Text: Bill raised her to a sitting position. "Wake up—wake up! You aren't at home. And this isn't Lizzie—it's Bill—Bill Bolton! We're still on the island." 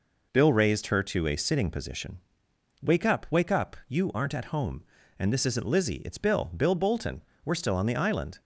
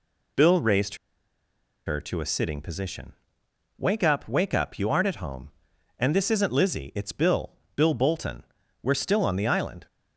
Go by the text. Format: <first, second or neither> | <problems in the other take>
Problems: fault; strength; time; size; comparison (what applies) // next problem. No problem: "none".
first | pauses between "raised" and "her"; noticeable; at 0.9 s; 0.91 s long